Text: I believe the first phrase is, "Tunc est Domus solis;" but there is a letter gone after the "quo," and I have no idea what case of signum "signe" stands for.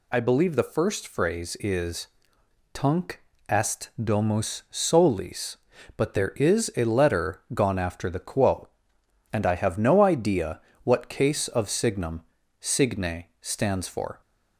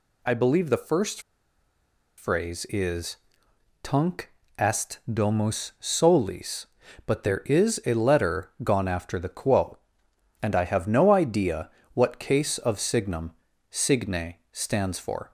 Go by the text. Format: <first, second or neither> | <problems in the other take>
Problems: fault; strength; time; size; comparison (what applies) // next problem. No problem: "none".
first | pauses between "first" and "phrase"; noticeable; at 1.2 s; 0.97 s long // pauses between "Tunc" and "est"; slight; at 4.2 s; 0.26 s long; slight in the first // pauses between "idea" and "what"; slight; at 11.6 s; 0.24 s long; slight in the first // pauses between "signum" and "signe"; at 13.3 s; 0.38 s long; also in the first // pauses between "signe" and "stands"; slight; at 14.3 s; 0.16 s long; slight in the first